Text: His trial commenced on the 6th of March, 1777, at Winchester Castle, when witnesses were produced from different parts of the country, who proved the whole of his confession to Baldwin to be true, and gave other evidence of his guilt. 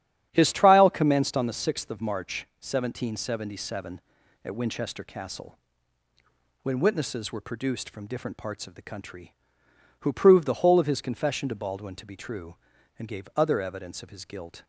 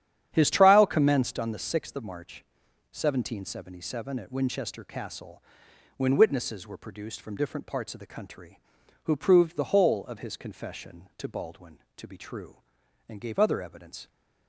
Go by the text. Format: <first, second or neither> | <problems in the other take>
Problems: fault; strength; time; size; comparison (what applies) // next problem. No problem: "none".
first | starts louder than the rest; strong; until 1.3 s; 9.5 dB; strong in the first // stops before "of his guilt"; at 14.0 s